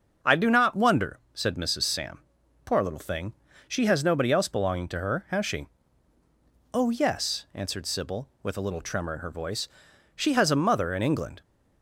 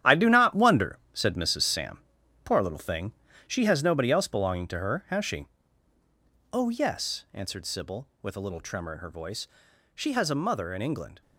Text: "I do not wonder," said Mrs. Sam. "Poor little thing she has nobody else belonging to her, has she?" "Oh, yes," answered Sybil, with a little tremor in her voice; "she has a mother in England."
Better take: first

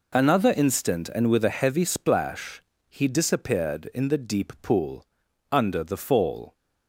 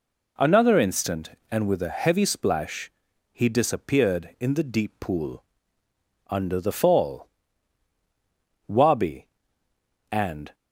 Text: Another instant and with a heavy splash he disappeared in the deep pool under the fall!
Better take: first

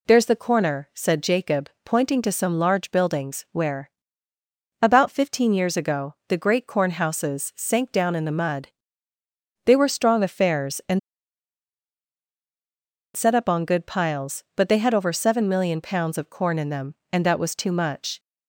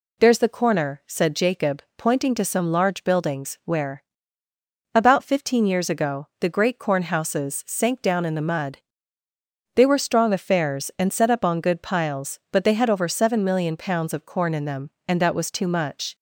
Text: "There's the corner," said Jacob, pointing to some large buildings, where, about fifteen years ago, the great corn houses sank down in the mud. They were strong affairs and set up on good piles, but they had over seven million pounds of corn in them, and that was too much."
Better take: second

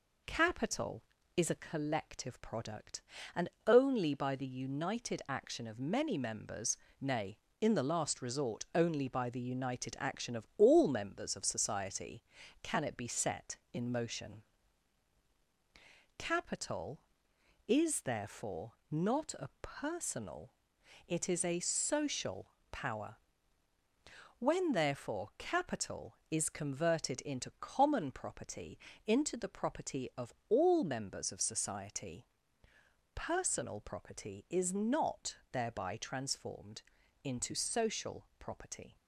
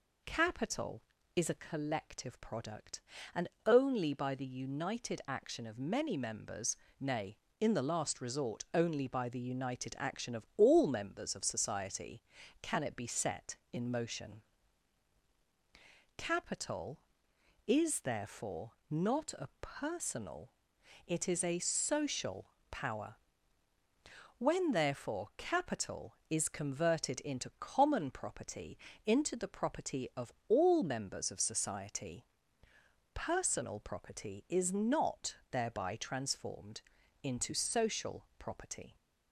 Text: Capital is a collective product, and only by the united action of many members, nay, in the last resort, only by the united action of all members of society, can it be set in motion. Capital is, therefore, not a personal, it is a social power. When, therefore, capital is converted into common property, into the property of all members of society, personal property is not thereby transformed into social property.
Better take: second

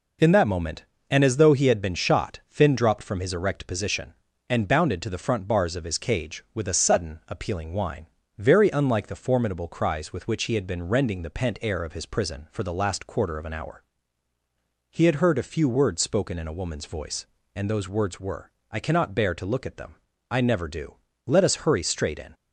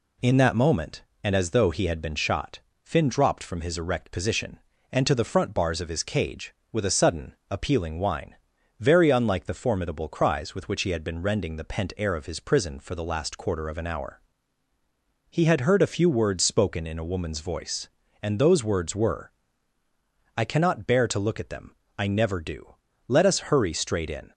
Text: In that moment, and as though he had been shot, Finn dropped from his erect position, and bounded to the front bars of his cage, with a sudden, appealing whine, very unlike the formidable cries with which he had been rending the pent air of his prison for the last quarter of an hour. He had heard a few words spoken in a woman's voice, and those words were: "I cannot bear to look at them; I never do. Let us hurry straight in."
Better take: first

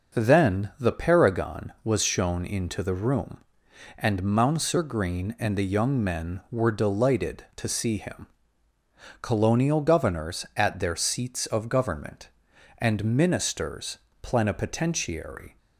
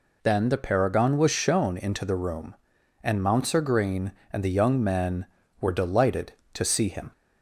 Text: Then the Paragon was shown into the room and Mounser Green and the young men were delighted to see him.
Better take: second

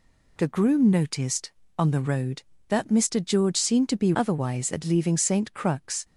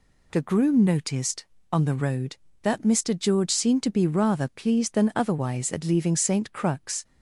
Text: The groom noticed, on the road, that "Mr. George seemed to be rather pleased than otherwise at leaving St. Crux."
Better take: second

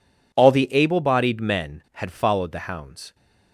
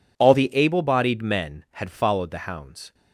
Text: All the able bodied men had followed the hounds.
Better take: neither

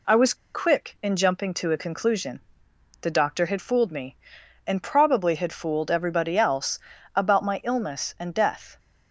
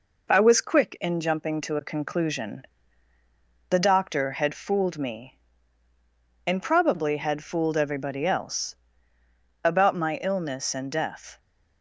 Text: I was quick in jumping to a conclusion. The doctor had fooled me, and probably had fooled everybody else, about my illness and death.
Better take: second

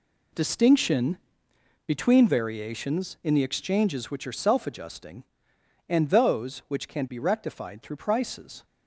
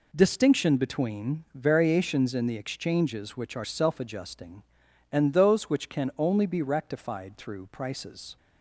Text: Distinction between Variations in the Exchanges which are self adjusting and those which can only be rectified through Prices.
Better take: second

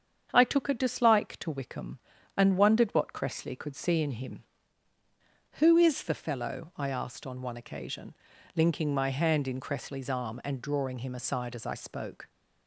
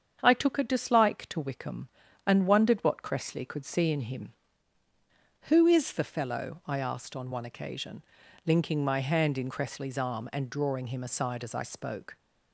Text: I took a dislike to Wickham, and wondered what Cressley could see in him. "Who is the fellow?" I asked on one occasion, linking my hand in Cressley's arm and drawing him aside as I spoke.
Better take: neither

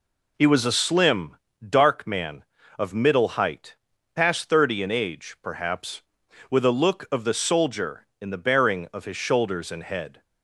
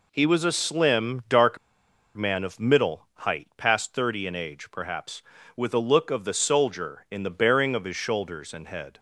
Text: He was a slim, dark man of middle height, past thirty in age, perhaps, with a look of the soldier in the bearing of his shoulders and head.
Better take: first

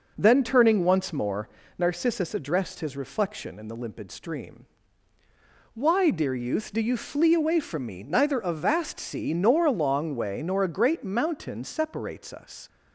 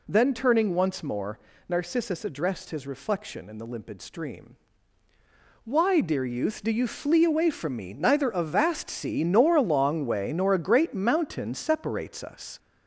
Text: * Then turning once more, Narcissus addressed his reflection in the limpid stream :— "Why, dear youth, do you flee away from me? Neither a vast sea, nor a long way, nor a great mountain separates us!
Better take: first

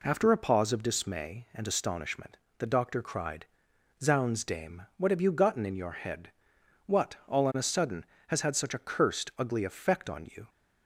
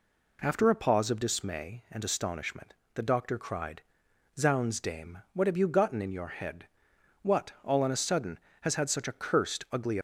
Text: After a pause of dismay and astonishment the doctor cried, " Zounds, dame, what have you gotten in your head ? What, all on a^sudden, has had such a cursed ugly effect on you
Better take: first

